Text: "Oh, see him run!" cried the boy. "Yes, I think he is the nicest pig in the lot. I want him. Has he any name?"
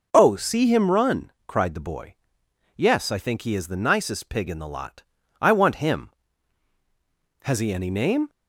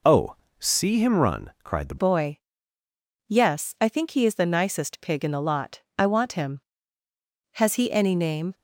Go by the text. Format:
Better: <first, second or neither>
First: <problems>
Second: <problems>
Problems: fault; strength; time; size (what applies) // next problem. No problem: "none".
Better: first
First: none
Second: changes voice at "boy"; from 1.9 s on; 6.6 s long